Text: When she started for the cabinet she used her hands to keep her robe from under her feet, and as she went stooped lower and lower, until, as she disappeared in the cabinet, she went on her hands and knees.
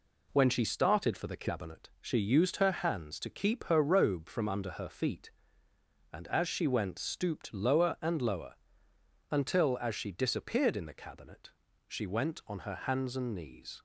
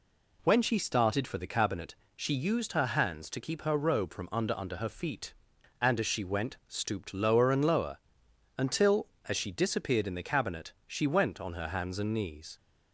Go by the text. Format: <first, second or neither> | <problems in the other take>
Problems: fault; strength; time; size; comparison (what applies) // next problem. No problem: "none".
first | pauses between "cabinet" and "she"; slight; at 1.9 s; 0.22 s long // says "under" twice; at 4.5 s